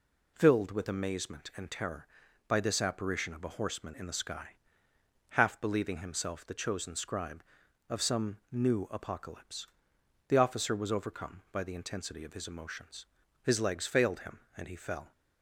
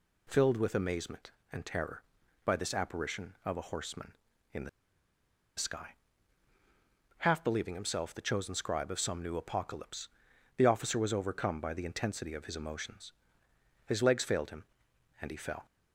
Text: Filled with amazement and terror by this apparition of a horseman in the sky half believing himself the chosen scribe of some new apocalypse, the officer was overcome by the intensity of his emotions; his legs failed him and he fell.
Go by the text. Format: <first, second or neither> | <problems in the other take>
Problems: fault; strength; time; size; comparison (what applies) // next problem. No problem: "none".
first | pauses between "the" and "sky"; noticeable; at 4.6 s; 0.87 s long // pauses between "sky" and "half"; strong; at 5.9 s; 1.2 s long; noticeable in the first